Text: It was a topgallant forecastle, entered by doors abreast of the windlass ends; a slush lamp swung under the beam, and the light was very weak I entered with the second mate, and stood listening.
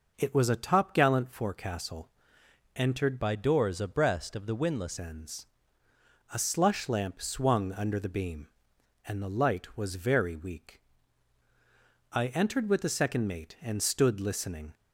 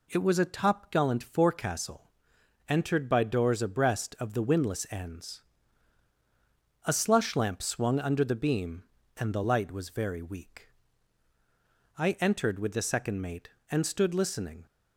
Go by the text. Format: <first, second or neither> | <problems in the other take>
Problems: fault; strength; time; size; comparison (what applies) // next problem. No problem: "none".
second | changes voice from "by" to "windlass"; from 3.1 to 4.9 s; 1.8 s long // pauses between "weak" and "I"; strong; at 10.7 s; 1.3 s long; strong in the second